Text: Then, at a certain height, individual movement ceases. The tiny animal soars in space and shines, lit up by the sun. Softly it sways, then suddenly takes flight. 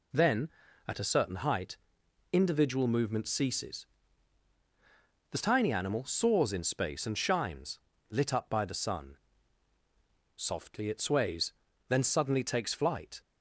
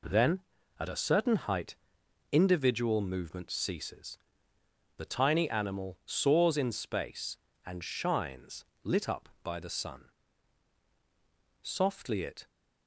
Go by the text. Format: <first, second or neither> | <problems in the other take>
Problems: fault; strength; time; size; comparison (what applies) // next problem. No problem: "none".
first | stops before "sways then suddenly takes flight"; at 12.4 s